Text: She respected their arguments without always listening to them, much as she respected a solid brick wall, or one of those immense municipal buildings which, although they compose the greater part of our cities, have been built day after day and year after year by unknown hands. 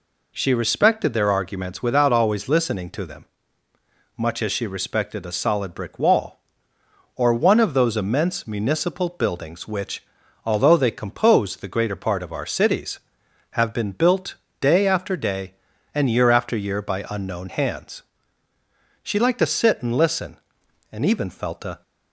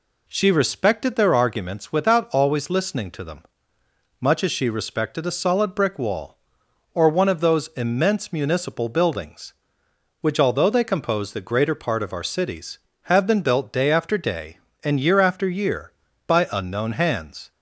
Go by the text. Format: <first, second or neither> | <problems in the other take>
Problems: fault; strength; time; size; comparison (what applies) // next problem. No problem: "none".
second | pauses between "built" and "day"; slight; at 14.3 s; 0.26 s long // goes on to say "She liked to sit and listen and even felt a"; strong; from 19.0 s on; 2.8 s long